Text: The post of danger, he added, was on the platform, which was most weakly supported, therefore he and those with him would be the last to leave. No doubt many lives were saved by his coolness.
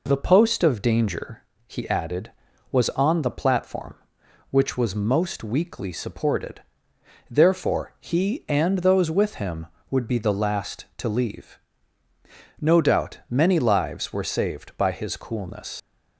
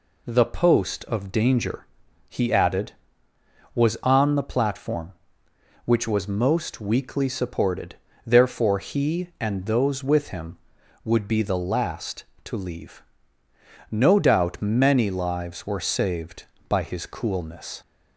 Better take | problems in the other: second | leaves "coolness" unfinished; at 15.7 s; 70 ms

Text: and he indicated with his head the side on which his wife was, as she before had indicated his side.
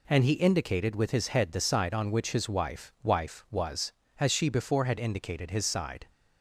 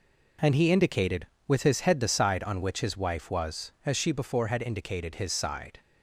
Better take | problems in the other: second | says "wife" twice; at 3.0 s

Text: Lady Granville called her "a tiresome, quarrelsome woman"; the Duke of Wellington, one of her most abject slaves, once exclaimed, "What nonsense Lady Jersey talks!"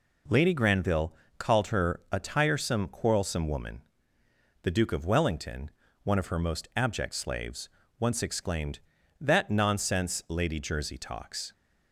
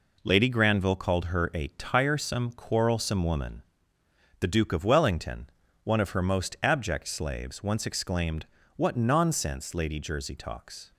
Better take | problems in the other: second | pauses between "Granville" and "called"; slight; at 1.1 s; 0.24 s long // says "That" for "What"; at 9.2 s

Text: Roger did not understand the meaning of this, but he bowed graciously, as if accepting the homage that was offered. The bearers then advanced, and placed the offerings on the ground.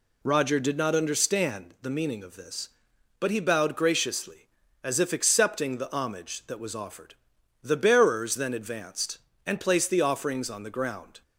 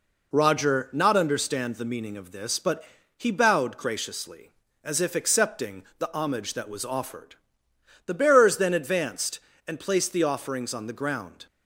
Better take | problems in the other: first | skips "did"; at 0.9 s // pauses between "but" and "he"; slight; at 2.8 s; 0.36 s long

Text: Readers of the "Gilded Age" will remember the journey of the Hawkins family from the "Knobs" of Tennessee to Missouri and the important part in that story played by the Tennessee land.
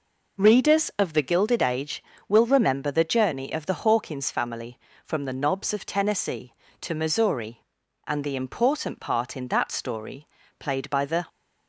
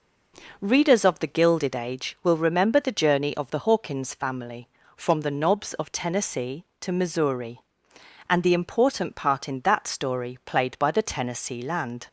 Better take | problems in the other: second | pauses between "story" and "played"; slight; at 10.2 s; 0.31 s long // stops before "Tennessee land"; at 11.2 s

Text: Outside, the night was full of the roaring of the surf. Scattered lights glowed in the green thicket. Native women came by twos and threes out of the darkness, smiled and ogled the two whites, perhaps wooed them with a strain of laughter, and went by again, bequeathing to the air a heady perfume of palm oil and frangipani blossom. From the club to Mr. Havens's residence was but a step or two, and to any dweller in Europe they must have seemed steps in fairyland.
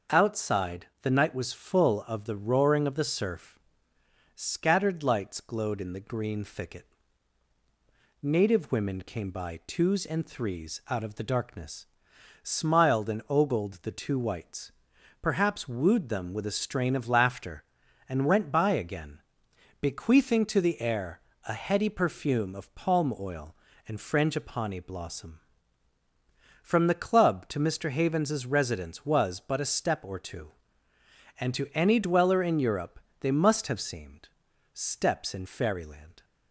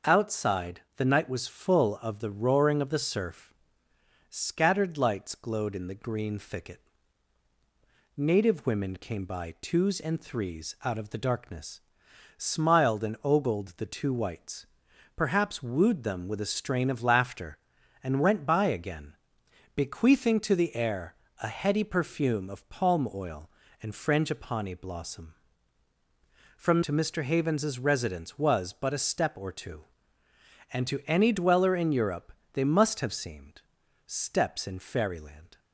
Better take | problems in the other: first | starts louder than the rest; until 1.2 s; 6.5 dB; also in the first // pauses between "air" and "a"; slight; at 21.1 s; 0.28 s long; slight in the first // skips "the club"; at 26.8 s // pauses between "Europe" and "they"; slight; at 32.3 s; 0.22 s long; slight in the first // pauses between "seemed" and "steps"; at 33.6 s; 0.44 s long; also in the first

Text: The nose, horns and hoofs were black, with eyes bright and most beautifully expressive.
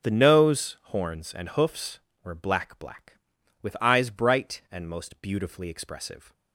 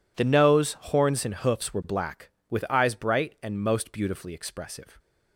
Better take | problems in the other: second | says "black" twice; at 2.7 s

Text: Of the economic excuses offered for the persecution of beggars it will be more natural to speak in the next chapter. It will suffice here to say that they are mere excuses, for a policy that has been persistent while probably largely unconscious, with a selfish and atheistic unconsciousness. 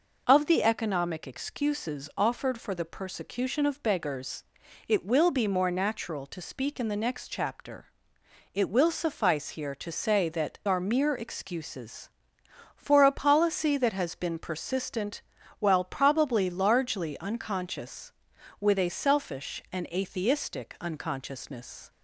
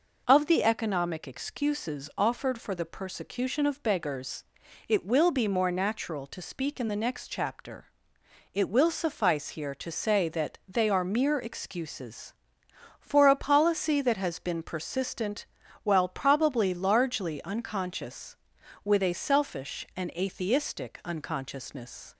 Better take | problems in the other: second | pauses between "beggars" and "it"; at 4.4 s; 0.42 s long; also in the second // skips "they"; at 10.6 s // pauses between "persistent" and "while"; slight; at 15.2 s; 0.36 s long; slight in the second

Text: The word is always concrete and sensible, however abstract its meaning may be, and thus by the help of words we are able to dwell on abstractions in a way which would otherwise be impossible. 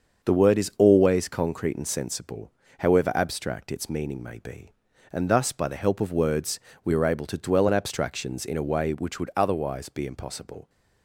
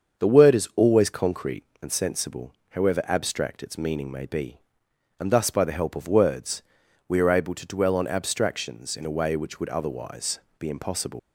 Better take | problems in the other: first | starts louder than the rest; until 1.2 s; 7 dB; also in the first // pauses between "words" and "we"; at 6.6 s; 0.44 s long; slight in the first // pauses between "otherwise" and "be"; slight; at 10.3 s; 0.18 s long // leaves "impossible" unfinished; at 11.1 s; 100 ms

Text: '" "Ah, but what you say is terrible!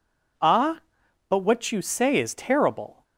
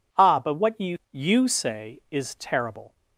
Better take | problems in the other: first | says "you" twice; at 1.1 s

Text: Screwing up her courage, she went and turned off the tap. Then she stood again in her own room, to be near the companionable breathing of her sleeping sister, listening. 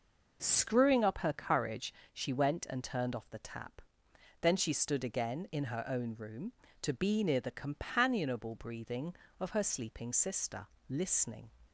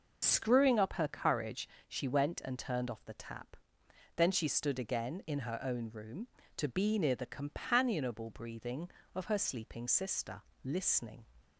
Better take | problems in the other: first | loses the start of "Screwing"; at 0.2 s; 75 ms

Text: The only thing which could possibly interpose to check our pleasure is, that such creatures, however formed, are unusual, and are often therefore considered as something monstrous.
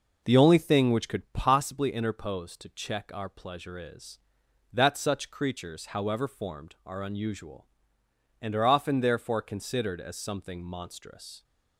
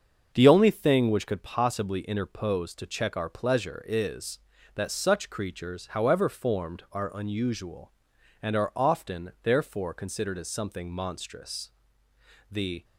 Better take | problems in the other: first | starts louder than the rest; until 1.3 s; 6.5 dB // goes on to say "The"; slight; from 12.4 s on; 0.34 s long

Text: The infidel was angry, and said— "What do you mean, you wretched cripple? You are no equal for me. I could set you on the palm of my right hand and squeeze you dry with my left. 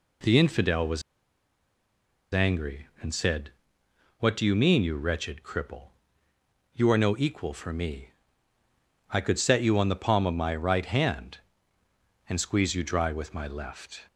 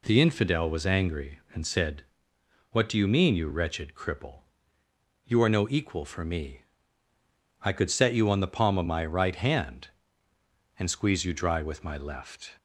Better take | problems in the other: second | pauses between "was" and "angry"; strong; at 1.0 s; 1.3 s long

